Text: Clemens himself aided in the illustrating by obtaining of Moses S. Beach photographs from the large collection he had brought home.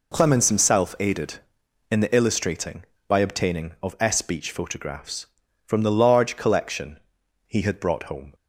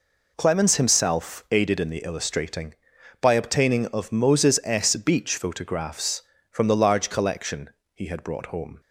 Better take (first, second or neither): second